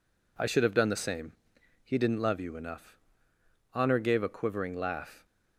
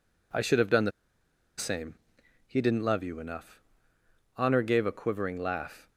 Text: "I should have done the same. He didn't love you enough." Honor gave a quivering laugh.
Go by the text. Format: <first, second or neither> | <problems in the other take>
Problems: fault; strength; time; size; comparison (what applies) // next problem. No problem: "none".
first | pauses between "the" and "same"; noticeable; at 0.9 s; 0.67 s long